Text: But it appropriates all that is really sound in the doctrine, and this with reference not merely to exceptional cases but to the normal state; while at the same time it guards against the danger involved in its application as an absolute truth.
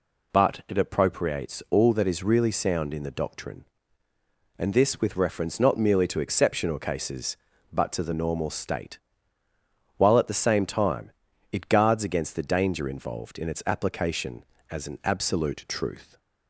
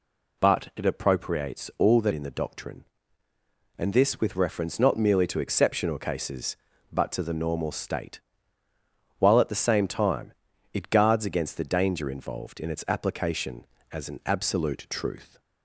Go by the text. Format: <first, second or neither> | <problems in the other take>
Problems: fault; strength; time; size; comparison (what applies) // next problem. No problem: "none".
first | skips "is really sound"; at 2.1 s // pauses between "time" and "it"; at 10.3 s; 0.38 s long; also in the first